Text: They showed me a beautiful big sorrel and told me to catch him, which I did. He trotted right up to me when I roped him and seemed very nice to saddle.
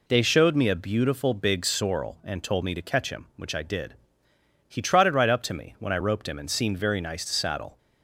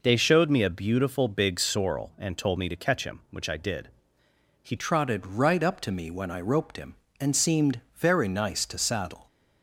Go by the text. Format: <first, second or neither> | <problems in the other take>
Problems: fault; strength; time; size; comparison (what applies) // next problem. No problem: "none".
first | changes voice at "trotted"; from 4.7 s on; 4.5 s long